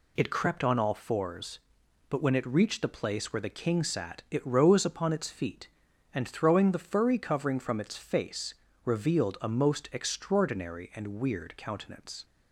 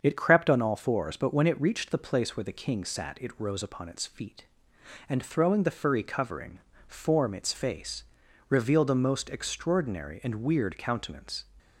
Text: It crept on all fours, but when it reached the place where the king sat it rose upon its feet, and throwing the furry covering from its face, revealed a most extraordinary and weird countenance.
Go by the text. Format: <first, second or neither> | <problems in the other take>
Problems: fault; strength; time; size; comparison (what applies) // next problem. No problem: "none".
first | starts louder than the rest; until 1.0 s; 7 dB // says "form" for "from"; at 6.8 s